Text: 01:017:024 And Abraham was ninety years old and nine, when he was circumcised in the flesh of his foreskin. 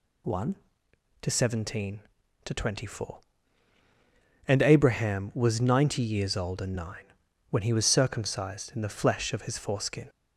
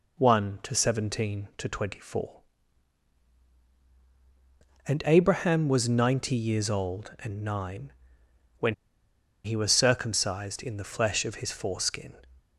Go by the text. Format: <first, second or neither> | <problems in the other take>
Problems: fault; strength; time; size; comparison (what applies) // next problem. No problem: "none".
first | pauses between "when" and "he"; noticeable; at 8.7 s; 0.70 s long